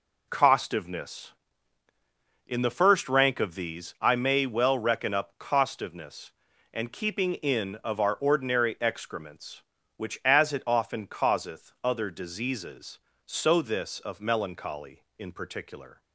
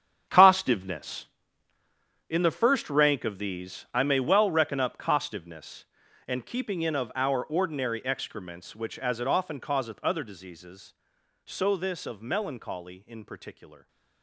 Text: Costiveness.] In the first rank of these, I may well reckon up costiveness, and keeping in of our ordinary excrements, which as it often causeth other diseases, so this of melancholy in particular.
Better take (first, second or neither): first